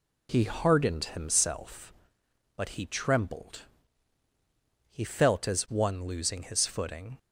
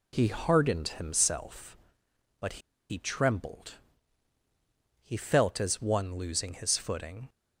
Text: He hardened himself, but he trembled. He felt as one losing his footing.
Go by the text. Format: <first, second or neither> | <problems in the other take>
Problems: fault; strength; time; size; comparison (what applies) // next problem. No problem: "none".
first | pauses between "but" and "he"; slight; at 2.6 s; 0.29 s long